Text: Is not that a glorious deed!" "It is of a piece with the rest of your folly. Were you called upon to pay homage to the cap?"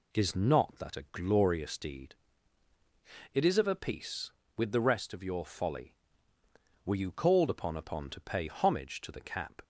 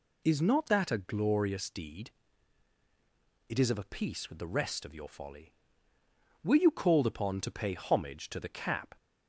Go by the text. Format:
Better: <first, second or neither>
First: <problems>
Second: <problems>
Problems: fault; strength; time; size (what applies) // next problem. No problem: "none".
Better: second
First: says "upon" twice; at 7.7 s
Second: none